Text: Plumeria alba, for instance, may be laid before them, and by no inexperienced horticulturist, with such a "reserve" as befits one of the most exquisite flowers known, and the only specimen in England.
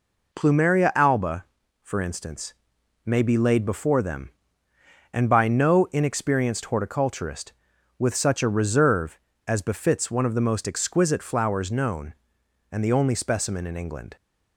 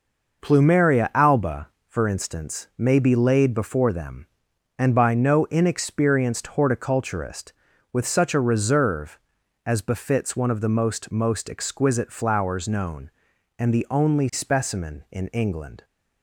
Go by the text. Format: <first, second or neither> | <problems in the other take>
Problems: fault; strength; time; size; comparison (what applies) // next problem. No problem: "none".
first | says "most" twice; at 11.1 s